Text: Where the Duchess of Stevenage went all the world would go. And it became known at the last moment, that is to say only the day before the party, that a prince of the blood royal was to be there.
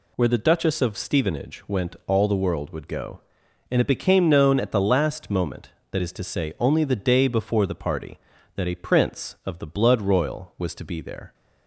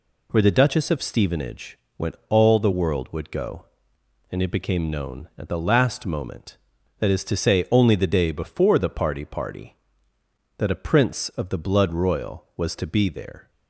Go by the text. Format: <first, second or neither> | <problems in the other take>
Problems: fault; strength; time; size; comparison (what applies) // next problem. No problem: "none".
first | pauses between "Stevenage" and "went"; slight; at 1.7 s; 0.20 s long // says "party" twice; at 9.2 s